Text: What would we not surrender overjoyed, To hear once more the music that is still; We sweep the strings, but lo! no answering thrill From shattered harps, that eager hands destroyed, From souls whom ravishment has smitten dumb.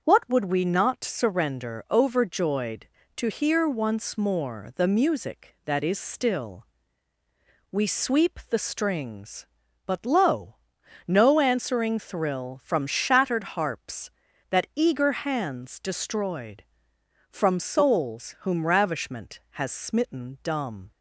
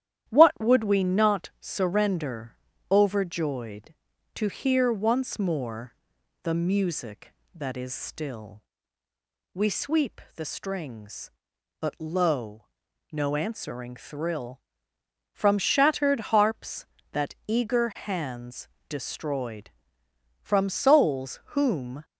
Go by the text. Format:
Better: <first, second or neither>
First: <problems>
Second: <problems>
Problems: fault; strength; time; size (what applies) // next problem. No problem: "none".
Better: first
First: starts louder than the rest; until 1.0 s; 6.5 dB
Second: starts louder than the rest; strong; until 1.3 s; 11 dB // pauses between "surrender" and "overjoyed"; slight; at 2.5 s; 0.34 s long // pauses between "more" and "the"; noticeable; at 5.9 s; 0.48 s long // pauses between "hands" and "destroyed"; slight; at 18.6 s; 0.18 s long // pauses between "souls" and "whom"; slight; at 21.3 s; 0.16 s long // stops before "ravishment has smitten dumb"; at 22.0 s